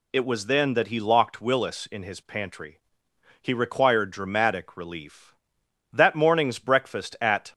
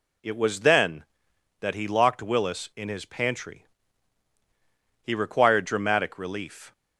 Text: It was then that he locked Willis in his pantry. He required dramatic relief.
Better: second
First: goes on to say "That morning's breakfast at"; from 5.9 s on; 1.6 s long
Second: none

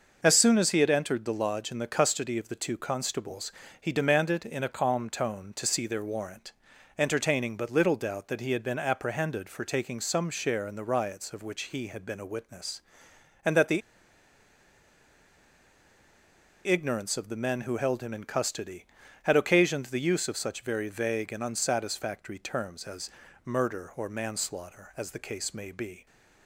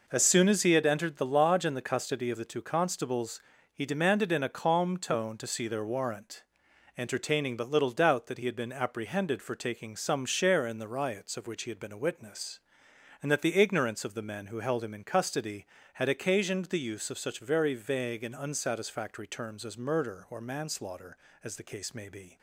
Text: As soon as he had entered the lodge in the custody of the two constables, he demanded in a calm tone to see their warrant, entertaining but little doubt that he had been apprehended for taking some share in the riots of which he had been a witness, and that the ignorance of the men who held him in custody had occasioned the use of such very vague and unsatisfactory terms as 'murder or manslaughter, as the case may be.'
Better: second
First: pauses between "the" and "ignorance"; strong; at 13.8 s; 2.8 s long // pauses between "as" and "murder"; slight; at 23.0 s; 0.34 s long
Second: none

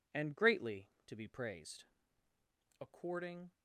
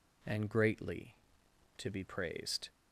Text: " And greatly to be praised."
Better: second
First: goes on to say "According"; noticeable; from 2.7 s on; 0.72 s long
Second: none

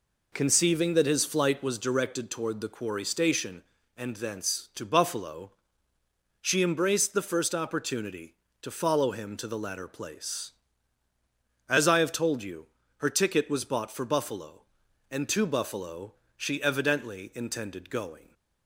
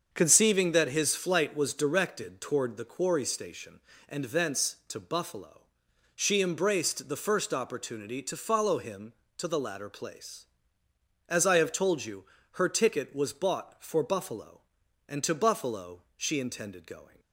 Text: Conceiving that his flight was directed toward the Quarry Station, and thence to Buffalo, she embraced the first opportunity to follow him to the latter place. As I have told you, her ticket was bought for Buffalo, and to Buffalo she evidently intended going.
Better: first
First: pauses between "Buffalo" and "she"; slight; at 16.1 s; 0.22 s long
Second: starts louder than the rest; until 1.1 s; 7 dB // pauses between "Buffalo" and "she"; slight; at 16.0 s; 0.16 s long // skips "evidently"; at 16.3 s

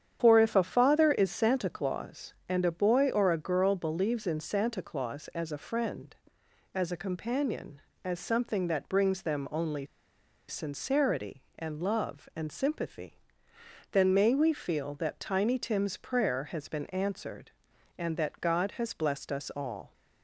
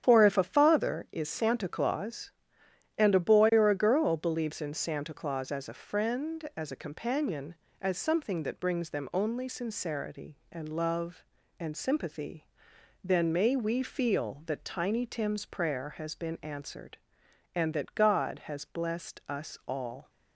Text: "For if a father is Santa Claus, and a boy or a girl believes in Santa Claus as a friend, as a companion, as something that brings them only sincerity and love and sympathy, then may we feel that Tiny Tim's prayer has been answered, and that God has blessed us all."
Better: second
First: starts louder than the rest; strong; until 1.2 s; 9 dB // pauses between "only" and "sincerity"; noticeable; at 9.8 s; 0.62 s long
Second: starts louder than the rest; strong; until 1.0 s; 9 dB

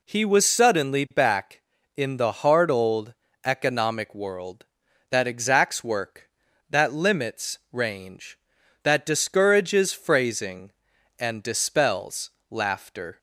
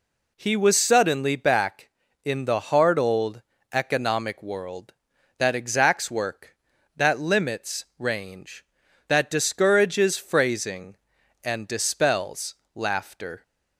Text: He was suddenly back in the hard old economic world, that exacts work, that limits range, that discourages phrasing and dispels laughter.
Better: neither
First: pauses between "old" and "economic"; slight; at 3.1 s; 0.30 s long // pauses between "dispels" and "laughter"; slight; at 12.2 s; 0.20 s long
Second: pauses between "old" and "economic"; slight; at 3.4 s; 0.30 s long // pauses between "dispels" and "laughter"; slight; at 12.5 s; 0.20 s long

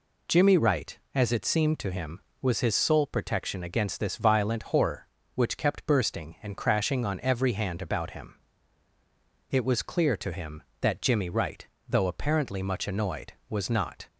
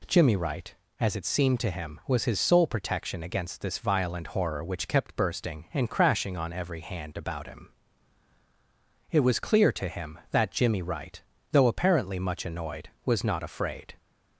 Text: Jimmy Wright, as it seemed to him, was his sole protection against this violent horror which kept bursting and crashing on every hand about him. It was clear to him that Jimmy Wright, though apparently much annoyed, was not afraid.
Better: second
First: stops before "afraid"; at 14.0 s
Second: none

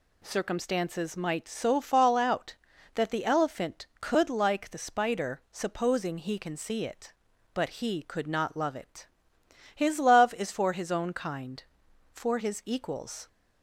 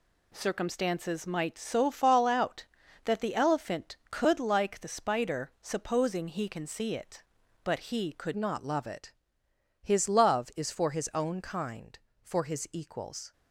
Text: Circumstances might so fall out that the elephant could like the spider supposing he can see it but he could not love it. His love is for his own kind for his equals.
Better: first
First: none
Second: changes voice at "not"; from 8.3 s on; 5.0 s long

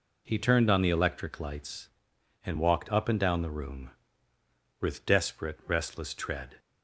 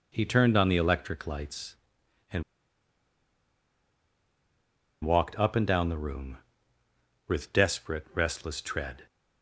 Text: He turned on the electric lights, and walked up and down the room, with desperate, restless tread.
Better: first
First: none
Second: pauses between "and" and "walked"; strong; at 2.4 s; 2.6 s long

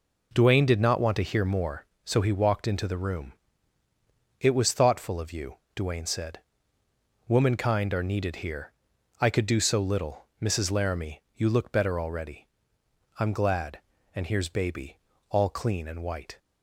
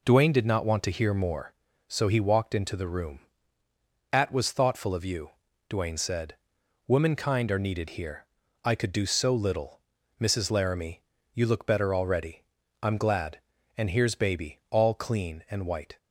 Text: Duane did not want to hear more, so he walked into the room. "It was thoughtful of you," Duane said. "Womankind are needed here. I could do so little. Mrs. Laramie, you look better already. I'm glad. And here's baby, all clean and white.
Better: first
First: none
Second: says "At" for "It"; at 4.1 s

